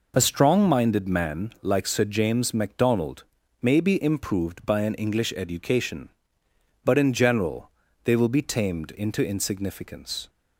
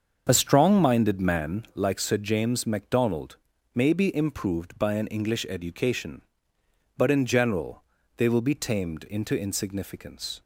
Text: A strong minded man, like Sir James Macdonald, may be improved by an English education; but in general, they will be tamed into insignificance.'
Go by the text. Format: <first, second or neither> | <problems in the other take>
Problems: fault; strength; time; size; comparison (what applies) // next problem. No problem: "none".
first | starts louder than the rest; until 1.8 s; 7 dB